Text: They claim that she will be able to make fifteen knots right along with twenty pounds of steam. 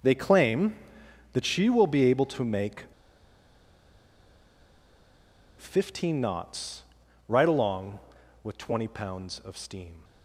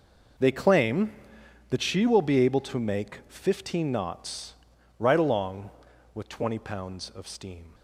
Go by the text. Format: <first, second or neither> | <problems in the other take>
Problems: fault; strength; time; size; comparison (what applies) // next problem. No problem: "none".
second | pauses between "make" and "fifteen"; strong; at 2.8 s; 2.7 s long // pauses between "knots" and "right"; at 6.8 s; 0.44 s long; also in the second